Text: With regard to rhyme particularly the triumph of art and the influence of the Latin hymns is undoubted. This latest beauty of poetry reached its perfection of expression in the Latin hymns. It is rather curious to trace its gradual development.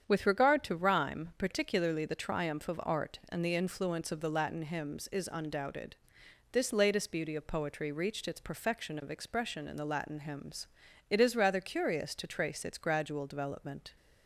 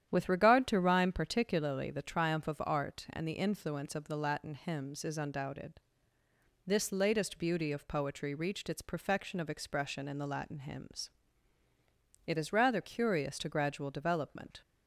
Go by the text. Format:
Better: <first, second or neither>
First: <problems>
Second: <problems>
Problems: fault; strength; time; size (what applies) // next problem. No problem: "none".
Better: first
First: starts louder than the rest; strong; until 1.0 s; 8 dB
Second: starts louder than the rest; strong; until 1.1 s; 10 dB // skips "trace its"; at 13.4 s